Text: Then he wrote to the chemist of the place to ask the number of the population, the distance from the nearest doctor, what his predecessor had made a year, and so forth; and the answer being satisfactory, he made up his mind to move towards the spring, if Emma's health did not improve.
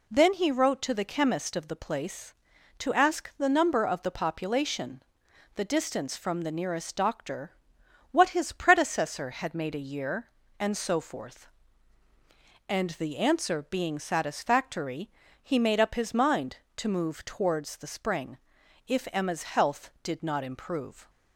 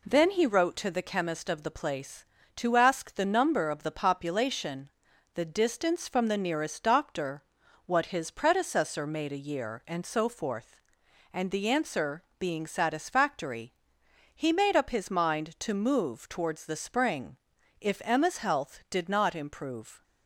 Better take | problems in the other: first | skips "had"; at 9.0 s // pauses between "answer" and "being"; slight; at 12.2 s; 0.16 s long

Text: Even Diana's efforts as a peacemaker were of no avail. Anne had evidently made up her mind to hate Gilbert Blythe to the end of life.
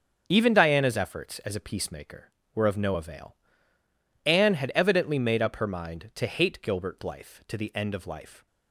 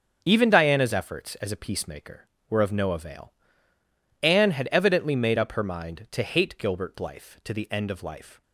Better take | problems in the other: neither | starts louder than the rest; the same in both

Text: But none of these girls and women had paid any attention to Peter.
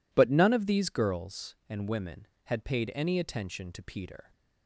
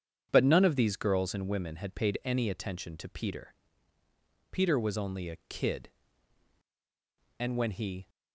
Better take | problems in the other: first | starts louder than the rest; strong; until 1.3 s; 8 dB // goes on to say "Peter was only a kid and when he"; strong; from 4.5 s on; 3.5 s long

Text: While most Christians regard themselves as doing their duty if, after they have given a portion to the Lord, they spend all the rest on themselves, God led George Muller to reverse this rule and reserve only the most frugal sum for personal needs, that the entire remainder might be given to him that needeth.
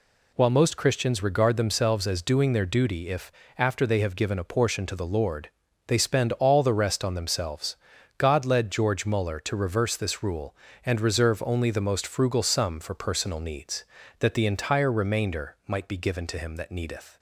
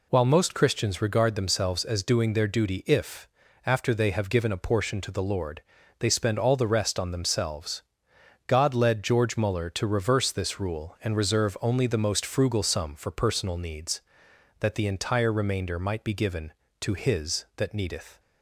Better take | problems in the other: first | says "his" for "him"; at 16.9 s

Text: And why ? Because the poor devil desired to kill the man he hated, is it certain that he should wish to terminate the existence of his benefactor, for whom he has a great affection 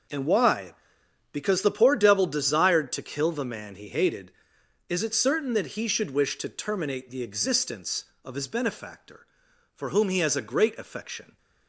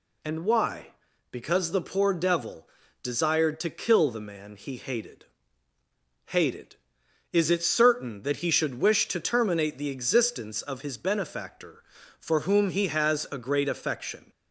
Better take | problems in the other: first | pauses between "devil" and "desired"; slight; at 2.6 s; 0.36 s long // says "hated" twice; at 6.2 s

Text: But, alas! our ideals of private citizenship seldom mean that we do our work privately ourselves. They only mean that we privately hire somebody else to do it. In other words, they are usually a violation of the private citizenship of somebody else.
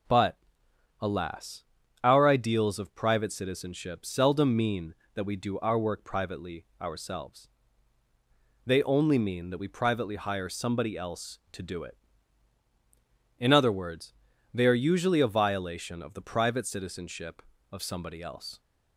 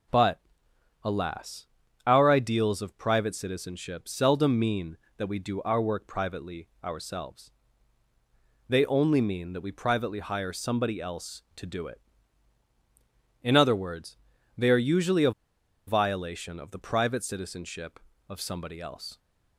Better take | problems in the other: first | pauses between "privately" and "ourselves"; slight; at 6.6 s; 0.16 s long; slight in the first // pauses between "a" and "violation"; noticeable; at 15.3 s; 0.55 s long

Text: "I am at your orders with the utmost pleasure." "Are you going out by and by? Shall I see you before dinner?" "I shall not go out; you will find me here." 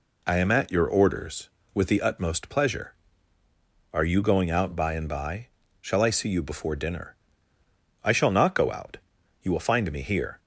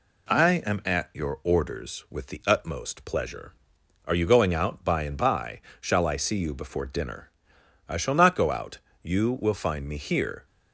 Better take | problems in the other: neither | none

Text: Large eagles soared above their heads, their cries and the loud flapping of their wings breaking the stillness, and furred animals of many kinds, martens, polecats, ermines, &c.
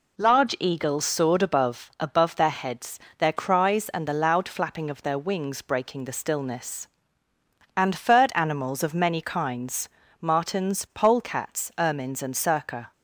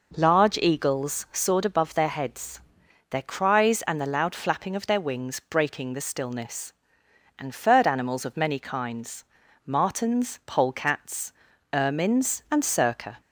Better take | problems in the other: second | says "above" twice; at 1.9 s

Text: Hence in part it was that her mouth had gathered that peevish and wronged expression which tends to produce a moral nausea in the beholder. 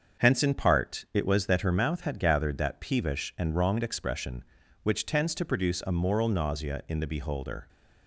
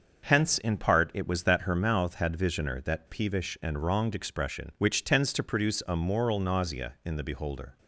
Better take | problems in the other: first | starts louder than the rest; until 1.2 s; 6.5 dB; also in the first // says "visioner" for "gathered"; at 2.3 s

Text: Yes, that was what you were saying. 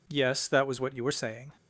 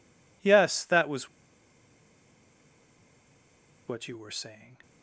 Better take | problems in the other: first | pauses between "was" and "what"; strong; at 1.2 s; 2.5 s long

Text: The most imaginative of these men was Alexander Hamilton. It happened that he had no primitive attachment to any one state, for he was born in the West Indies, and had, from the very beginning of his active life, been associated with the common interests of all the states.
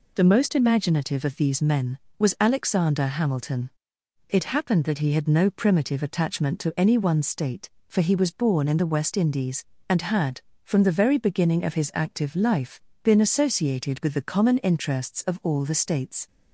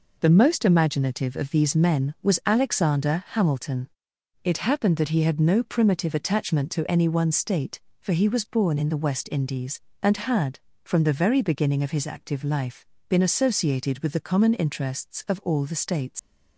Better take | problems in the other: first | leaves "states" unfinished; at 16.1 s; 105 ms

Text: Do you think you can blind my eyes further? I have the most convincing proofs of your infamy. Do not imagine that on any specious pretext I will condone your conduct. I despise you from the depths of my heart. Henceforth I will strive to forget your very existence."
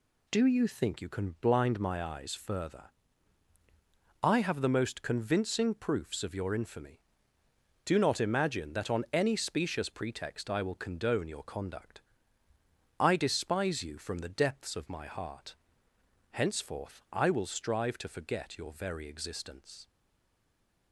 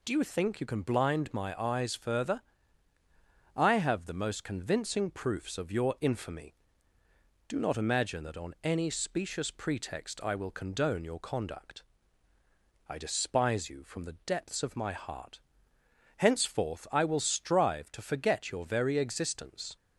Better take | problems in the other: second | stays silent after the last word; from 19.8 s on; 1.1 s long

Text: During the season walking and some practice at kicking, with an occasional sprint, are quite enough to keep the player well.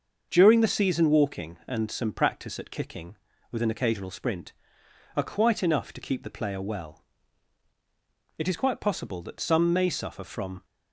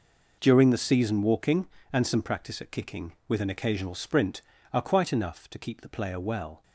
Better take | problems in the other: second | starts louder than the rest; until 1.3 s; 6.5 dB // goes on to say "It is quite possible that some may suffer from"; strong; from 8.3 s on; 2.2 s long

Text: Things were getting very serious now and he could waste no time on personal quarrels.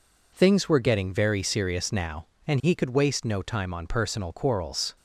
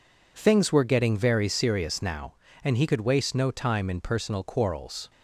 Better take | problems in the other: first | says "in" for "on"; at 3.8 s

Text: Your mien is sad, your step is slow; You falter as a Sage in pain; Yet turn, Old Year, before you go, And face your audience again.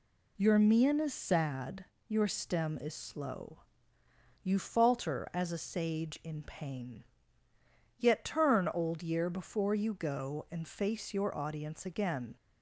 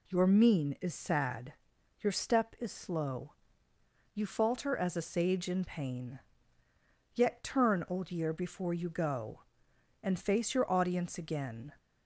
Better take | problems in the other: second | says "stem" for "step"; at 2.2 s

